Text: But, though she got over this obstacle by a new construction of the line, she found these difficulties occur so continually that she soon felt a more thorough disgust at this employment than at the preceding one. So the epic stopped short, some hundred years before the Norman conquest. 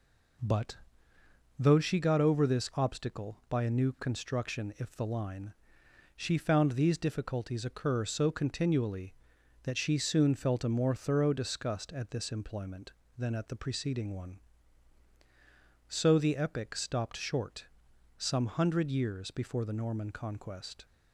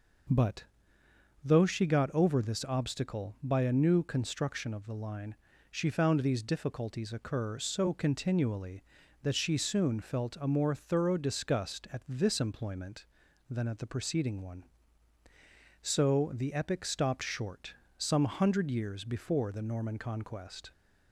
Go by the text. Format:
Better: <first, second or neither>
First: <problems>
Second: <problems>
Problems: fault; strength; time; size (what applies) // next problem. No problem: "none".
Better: second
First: says "if" for "of"; at 4.7 s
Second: none